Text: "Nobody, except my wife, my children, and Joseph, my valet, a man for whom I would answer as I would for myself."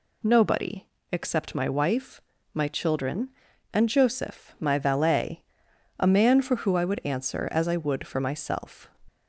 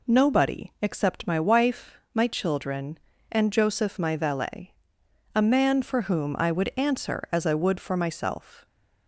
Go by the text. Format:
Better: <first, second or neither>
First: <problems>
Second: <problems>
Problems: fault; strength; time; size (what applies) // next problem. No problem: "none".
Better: second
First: says "who" for "whom"; at 6.5 s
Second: none